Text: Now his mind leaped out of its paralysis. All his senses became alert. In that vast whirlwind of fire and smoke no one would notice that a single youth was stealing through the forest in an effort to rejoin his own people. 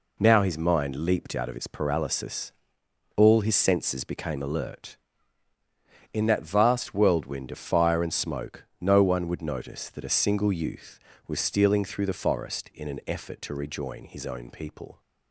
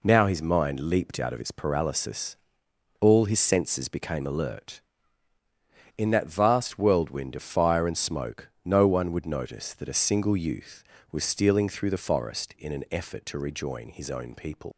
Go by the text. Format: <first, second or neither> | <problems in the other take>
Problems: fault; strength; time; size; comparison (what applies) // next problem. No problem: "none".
first | pauses between "smoke" and "no"; slight; at 8.4 s; 0.16 s long; slight in the first // leaves "people" unfinished; at 14.7 s; 125 ms